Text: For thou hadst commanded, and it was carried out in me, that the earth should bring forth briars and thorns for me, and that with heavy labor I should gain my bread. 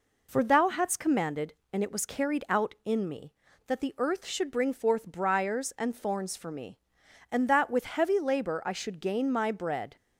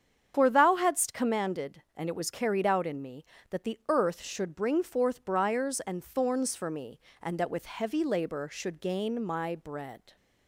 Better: first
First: none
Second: starts louder than the rest; strong; until 1.3 s; 8 dB // skips "I"; at 8.5 s

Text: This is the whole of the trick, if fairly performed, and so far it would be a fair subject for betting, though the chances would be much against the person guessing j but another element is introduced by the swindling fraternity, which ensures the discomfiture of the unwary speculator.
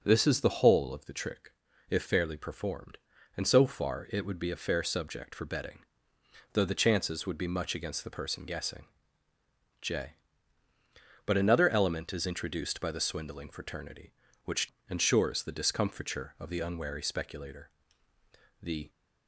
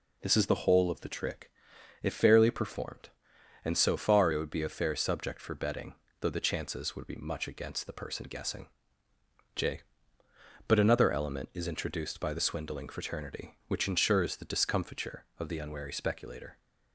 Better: second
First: pauses between "guessing" and "j"; noticeable; at 8.8 s; 0.94 s long // pauses between "which" and "ensures"; slight; at 14.7 s; 0.18 s long // goes on to say "The"; slight; from 18.6 s on; 0.28 s long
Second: pauses between "guessing" and "j"; noticeable; at 8.6 s; 0.88 s long

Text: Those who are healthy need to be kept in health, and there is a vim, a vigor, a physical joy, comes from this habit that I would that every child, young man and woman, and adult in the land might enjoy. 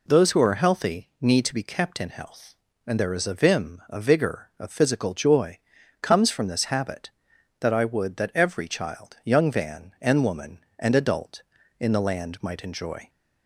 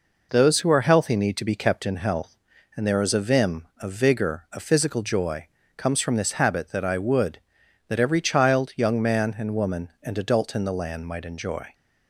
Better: second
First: says "van" for "man"; at 9.5 s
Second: none

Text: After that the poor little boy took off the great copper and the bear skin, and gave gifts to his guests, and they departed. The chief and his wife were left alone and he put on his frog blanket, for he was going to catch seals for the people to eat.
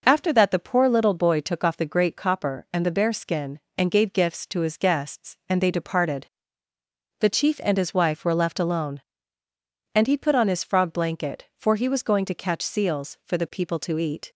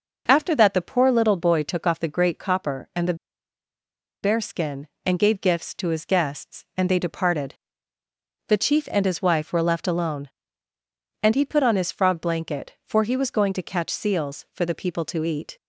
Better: first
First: none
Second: pauses between "the" and "bear"; at 3.1 s; 1.0 s long

